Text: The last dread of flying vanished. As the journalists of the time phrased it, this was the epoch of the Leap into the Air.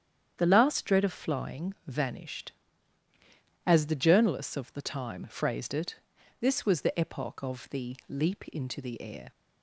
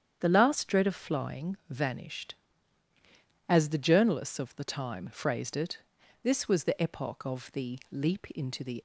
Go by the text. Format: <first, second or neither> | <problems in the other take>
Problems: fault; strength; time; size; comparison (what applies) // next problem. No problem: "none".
first | starts louder than the rest; strong; until 1.2 s; 9 dB; strong in the first // stops before "Air"; at 8.7 s